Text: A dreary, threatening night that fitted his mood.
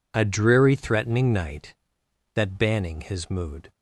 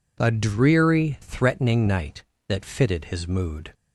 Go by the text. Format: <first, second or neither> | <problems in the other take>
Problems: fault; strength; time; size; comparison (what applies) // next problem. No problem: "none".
second | says "banning" for "fitted"; at 2.5 s